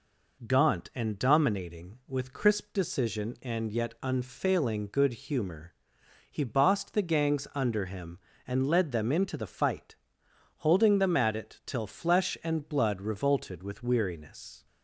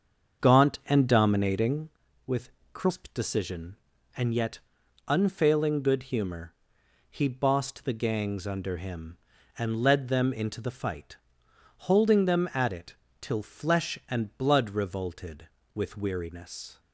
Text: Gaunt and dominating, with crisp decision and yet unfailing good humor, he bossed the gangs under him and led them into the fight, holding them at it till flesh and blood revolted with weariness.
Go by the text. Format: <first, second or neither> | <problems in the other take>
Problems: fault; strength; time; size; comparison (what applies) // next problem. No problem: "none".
first | starts louder than the rest; until 2.0 s; 7 dB // pauses between "with" and "crisp"; slight; at 2.4 s; 0.24 s long // pauses between "yet" and "unfailing"; noticeable; at 4.5 s; 0.48 s long // pauses between "it" and "till"; slight; at 12.9 s; 0.26 s long